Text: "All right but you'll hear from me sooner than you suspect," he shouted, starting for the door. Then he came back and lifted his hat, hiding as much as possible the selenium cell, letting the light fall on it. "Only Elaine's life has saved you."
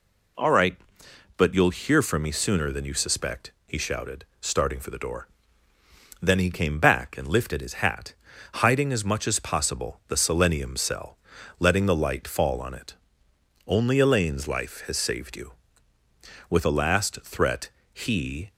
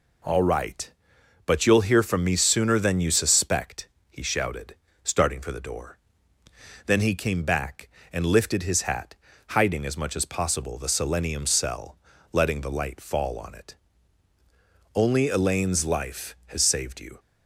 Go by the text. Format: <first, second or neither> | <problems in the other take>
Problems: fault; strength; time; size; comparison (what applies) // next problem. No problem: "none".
second | goes on to say "With a last threat he"; strong; from 16.4 s on; 2.0 s long